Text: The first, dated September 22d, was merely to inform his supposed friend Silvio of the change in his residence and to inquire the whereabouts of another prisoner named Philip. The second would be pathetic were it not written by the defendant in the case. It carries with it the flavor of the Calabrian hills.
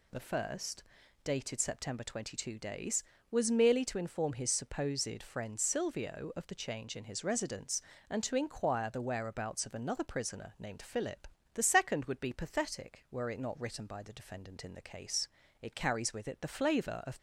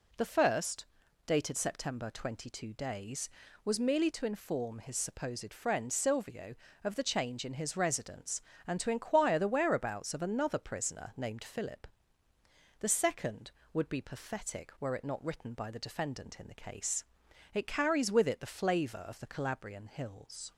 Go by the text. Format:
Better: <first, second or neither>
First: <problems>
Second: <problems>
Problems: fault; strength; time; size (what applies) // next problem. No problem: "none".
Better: second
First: stops before "the Calabrian hills"; at 17.1 s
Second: none